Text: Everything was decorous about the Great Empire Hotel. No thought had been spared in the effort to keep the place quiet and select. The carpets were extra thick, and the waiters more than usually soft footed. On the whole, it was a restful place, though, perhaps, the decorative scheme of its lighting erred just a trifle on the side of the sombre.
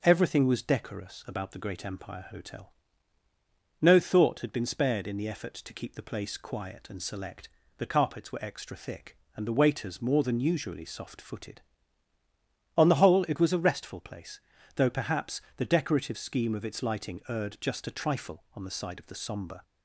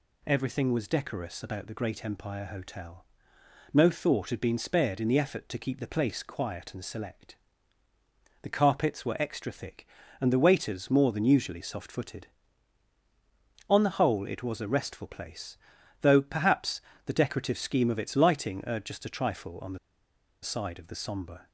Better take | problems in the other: first | pauses between "the" and "side"; noticeable; at 19.7 s; 0.64 s long

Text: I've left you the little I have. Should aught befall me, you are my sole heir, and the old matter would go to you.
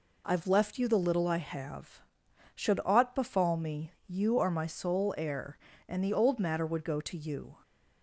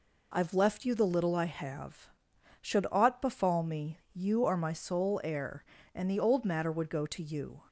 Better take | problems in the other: neither | none

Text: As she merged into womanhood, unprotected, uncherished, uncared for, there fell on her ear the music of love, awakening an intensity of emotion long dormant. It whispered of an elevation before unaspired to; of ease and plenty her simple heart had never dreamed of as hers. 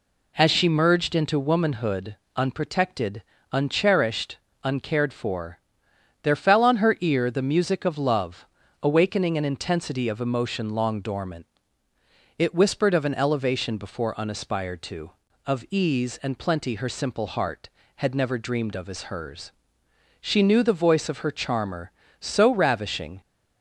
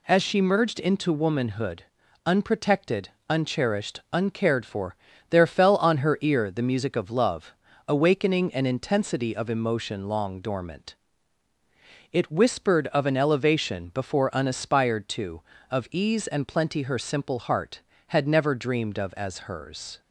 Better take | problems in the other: second | goes on to say "She knew the voice of her charmer so ravishing"; strong; from 20.2 s on; 3.0 s long

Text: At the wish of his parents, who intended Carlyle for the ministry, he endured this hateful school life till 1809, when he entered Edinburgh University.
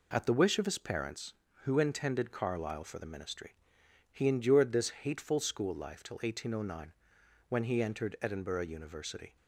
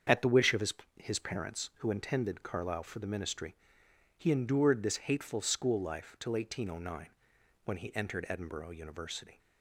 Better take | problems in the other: first | starts louder than the rest; strong; until 1.3 s; 7.5 dB // says "his" twice; at 0.9 s

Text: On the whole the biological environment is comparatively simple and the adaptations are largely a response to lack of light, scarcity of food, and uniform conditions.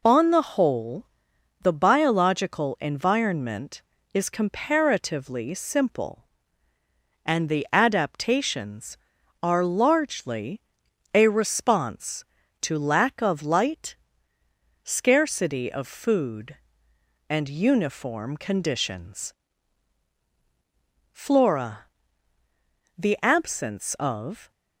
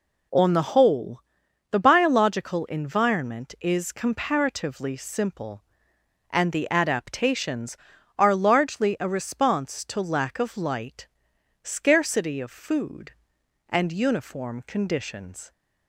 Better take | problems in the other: second | pauses between "whole" and "the"; noticeable; at 1.0 s; 0.58 s long; noticeable in the second // pauses between "largely" and "a"; noticeable; at 10.5 s; 0.54 s long // goes on to say "Flora The absence of"; strong; from 21.1 s on; 3.4 s long

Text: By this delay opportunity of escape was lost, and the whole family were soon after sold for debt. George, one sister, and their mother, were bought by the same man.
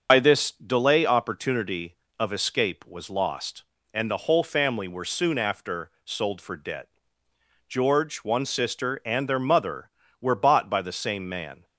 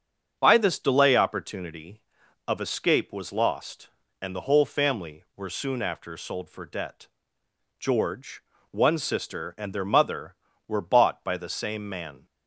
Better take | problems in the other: second | loses the start of "By"; at 0.0 s; 75 ms // starts louder than the rest; noticeable; until 1.1 s; 6 dB; strong in the second // pauses between "after" and "sold"; slight; at 5.9 s; 0.16 s long

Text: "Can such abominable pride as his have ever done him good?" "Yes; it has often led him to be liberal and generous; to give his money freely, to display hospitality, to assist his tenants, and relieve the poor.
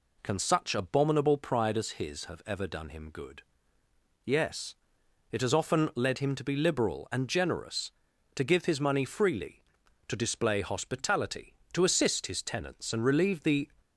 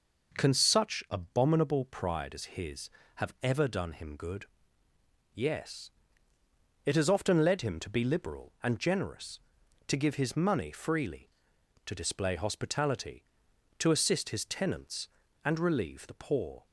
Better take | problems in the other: second | stops before "poor"; at 13.7 s

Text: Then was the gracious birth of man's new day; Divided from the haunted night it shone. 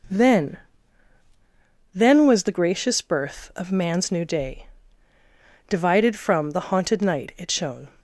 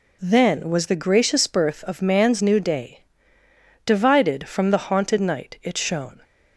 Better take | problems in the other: second | says "Then" twice; at 1.9 s

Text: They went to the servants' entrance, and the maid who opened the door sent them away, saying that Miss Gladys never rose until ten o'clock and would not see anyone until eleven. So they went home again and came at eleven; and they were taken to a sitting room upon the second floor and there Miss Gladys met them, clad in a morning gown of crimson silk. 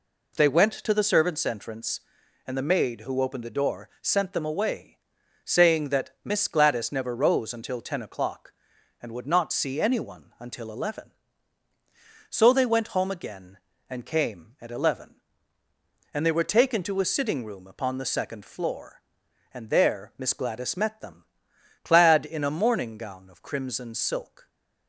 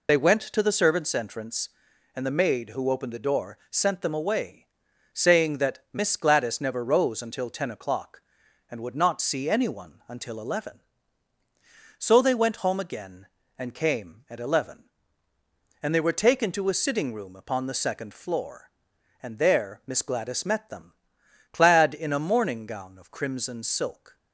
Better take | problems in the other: first | loses the start of "They"; at 0.0 s; 55 ms

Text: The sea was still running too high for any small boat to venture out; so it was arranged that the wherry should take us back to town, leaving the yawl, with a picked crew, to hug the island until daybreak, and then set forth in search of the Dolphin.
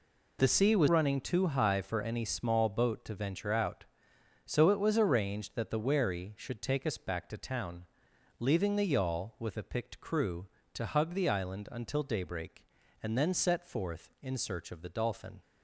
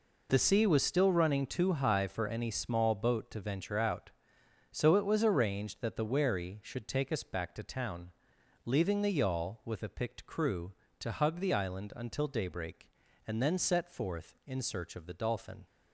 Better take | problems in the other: second | skips "still"; at 0.8 s

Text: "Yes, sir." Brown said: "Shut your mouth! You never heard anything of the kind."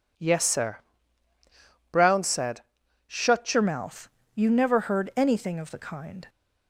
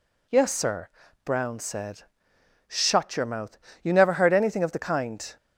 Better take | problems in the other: second | changes voice at "your"; from 3.5 s on; 2.7 s long

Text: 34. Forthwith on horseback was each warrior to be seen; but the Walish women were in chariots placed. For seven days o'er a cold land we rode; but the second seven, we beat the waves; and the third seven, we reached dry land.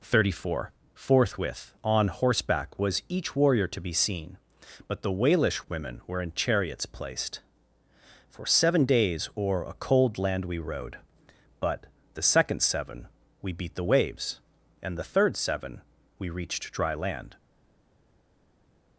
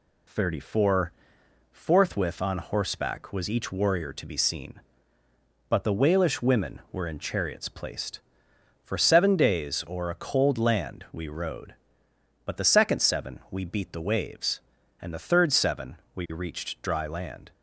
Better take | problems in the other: second | pauses between "but" and "the"; slight; at 11.8 s; 0.26 s long // stays silent after the last word; noticeable; from 17.3 s on; 1.6 s long

